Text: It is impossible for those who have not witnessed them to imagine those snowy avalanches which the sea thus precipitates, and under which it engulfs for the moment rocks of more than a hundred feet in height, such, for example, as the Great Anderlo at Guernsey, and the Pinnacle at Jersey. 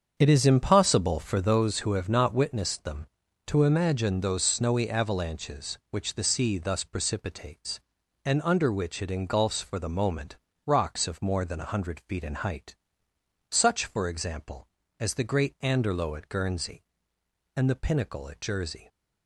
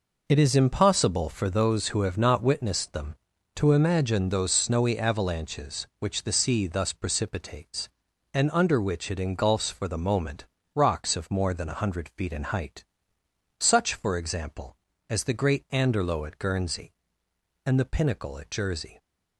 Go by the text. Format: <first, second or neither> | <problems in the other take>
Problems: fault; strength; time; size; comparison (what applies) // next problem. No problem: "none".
second | starts louder than the rest; strong; until 1.8 s; 7 dB // pauses between "moment" and "rocks"; slight; at 10.3 s; 0.28 s long; slight in the second